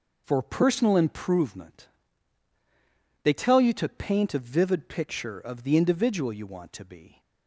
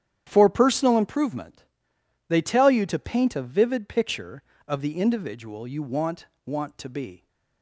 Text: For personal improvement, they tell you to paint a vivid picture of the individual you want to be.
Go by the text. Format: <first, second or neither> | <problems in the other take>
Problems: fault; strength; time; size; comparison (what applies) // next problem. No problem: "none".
first | starts louder than the rest; strong; until 1.2 s; 10 dB // says "want" twice; at 6.4 s